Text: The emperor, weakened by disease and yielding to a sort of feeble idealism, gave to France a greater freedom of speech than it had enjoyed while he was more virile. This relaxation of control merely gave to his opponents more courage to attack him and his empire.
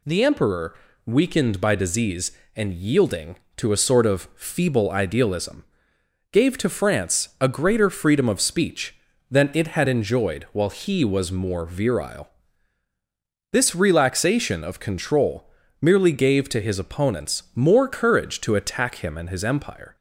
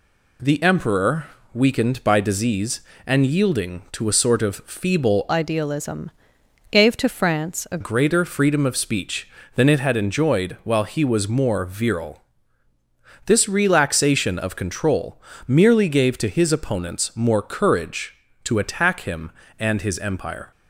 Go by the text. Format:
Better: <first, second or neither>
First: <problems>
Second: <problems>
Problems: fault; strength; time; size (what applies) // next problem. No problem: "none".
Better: first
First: pauses between "control" and "merely"; slight; at 15.5 s; 0.30 s long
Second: changes voice from "idealism" to "a"; from 5.2 to 7.7 s; 2.5 s long // pauses between "control" and "merely"; slight; at 15.1 s; 0.28 s long